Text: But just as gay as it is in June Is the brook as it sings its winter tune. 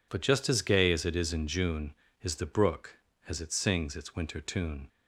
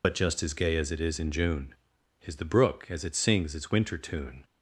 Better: first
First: none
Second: loses the start of "But"; at 0.0 s; 50 ms

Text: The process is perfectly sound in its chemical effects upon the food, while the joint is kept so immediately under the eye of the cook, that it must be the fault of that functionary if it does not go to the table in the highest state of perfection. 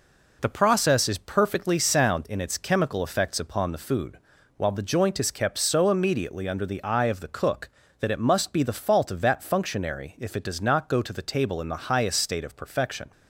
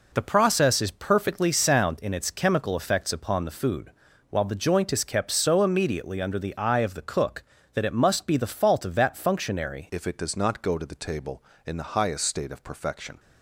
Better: first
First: none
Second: changes voice at "if"; from 9.8 s on; 3.3 s long

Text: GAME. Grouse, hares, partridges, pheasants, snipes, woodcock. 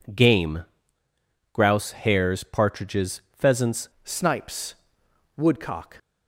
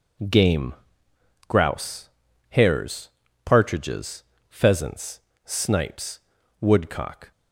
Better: second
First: changes voice at "snipes"; from 4.0 s on; 1.9 s long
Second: none

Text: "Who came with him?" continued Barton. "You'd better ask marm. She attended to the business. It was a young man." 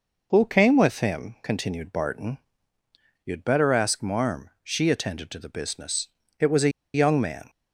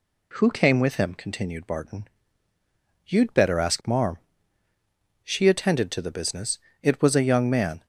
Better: second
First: pauses between "a" and "young"; slight; at 6.6 s; 0.25 s long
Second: none

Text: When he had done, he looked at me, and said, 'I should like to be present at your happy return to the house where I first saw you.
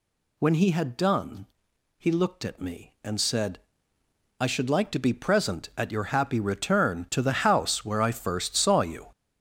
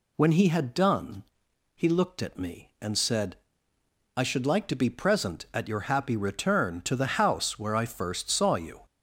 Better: second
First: gets louder; strong; throughout; 8.5 dB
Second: none

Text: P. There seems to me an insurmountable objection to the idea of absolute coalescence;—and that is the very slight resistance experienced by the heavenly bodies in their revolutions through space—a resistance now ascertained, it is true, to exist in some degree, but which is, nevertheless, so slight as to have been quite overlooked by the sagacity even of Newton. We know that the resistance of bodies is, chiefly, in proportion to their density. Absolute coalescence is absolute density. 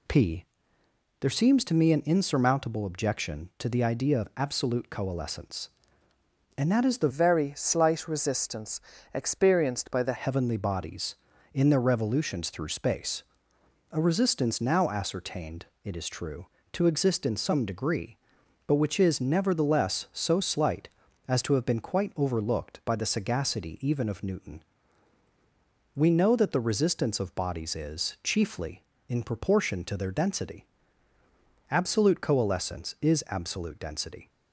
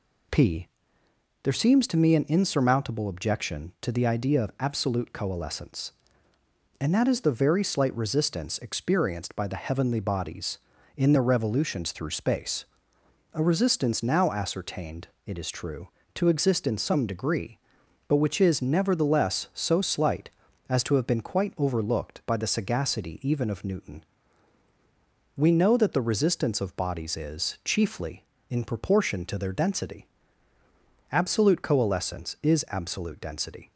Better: second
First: changes voice from "very" to "the"; from 7.0 to 10.1 s; 3.1 s long // pauses between "resistance" and "experienced"; slight; at 8.8 s; 0.32 s long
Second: none

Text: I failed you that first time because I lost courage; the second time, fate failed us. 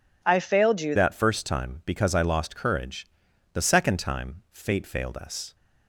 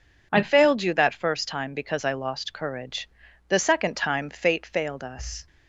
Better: second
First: changes voice at "that"; from 0.9 s on; 4.6 s long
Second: none

